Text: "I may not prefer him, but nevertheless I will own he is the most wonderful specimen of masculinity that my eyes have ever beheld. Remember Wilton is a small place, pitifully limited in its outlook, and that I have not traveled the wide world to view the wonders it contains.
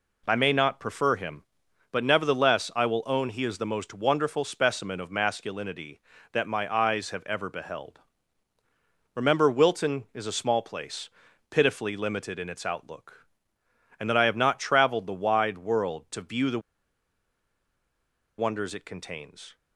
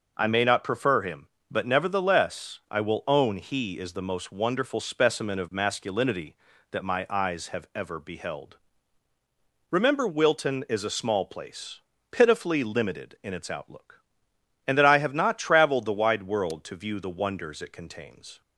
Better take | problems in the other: second | pauses between "the" and "wonders"; strong; at 16.6 s; 1.7 s long

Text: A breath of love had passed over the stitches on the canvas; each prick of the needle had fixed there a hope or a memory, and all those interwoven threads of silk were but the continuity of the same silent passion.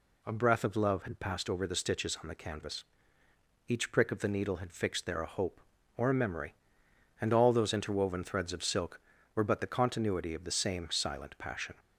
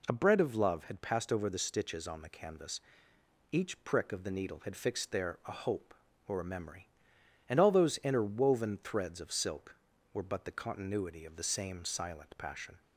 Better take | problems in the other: first | says "bread" for "breath"; at 0.1 s

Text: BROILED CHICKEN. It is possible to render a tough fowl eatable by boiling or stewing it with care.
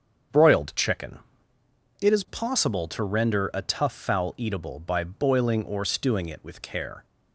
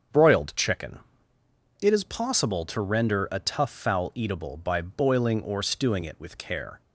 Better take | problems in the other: neither | starts louder than the rest; strong; the same in both

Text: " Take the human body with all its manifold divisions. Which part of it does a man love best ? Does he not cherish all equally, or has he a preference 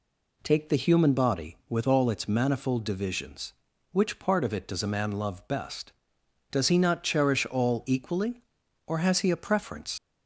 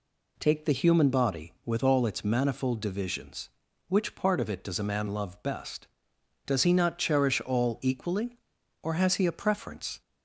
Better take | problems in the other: second | leaves "preference" unfinished; at 9.9 s; 75 ms

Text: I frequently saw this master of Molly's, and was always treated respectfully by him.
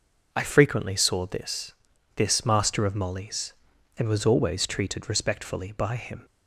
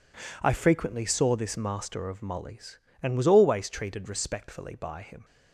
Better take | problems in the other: second | says "this" twice; at 2.1 s

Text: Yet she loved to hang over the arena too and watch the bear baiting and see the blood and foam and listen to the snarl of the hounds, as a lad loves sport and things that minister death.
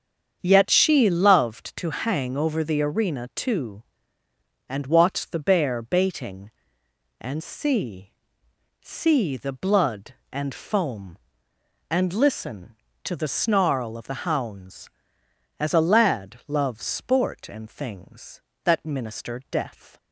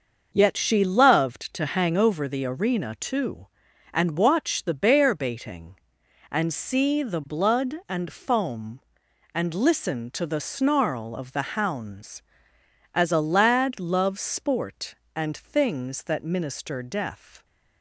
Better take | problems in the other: second | starts louder than the rest; strong; until 1.4 s; 7.5 dB; also in the second // says "see" twice; at 8.8 s

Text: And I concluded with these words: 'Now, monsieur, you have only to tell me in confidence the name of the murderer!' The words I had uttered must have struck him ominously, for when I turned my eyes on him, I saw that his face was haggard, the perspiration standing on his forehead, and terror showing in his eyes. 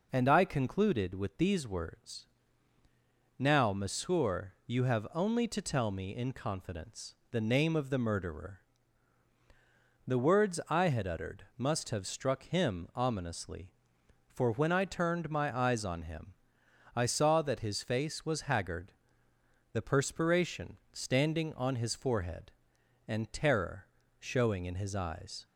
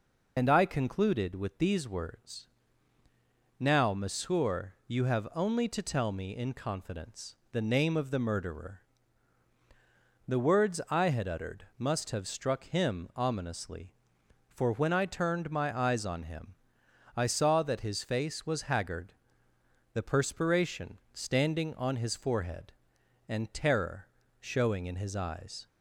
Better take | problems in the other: first | loses the start of "And"; at 0.3 s; 45 ms // pauses between "confidence" and "the"; slight; at 7.3 s; 0.16 s long; slight in the first // pauses between "terror" and "showing"; slight; at 24.0 s; 0.34 s long; slight in the first

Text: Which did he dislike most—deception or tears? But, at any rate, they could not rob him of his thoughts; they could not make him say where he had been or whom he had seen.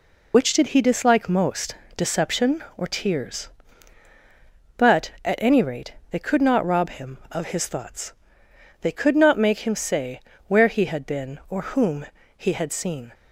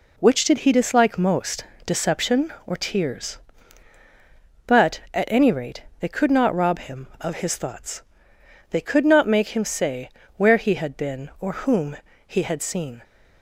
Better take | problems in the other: second | loses the start of "Which"; at 0.3 s; 75 ms // pauses between "say" and "where"; slight; at 10.1 s; 0.28 s long; slight in the second // pauses between "whom" and "he"; slight; at 12.0 s; 0.32 s long; slight in the second

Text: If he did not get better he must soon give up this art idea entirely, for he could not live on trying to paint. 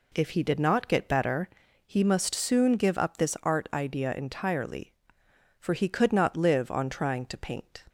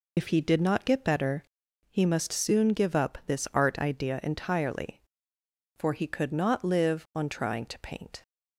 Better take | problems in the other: first | loses the start of "If"; at 0.1 s; 55 ms // pauses between "better" and "he"; noticeable; at 1.4 s; 0.46 s long; also in the first

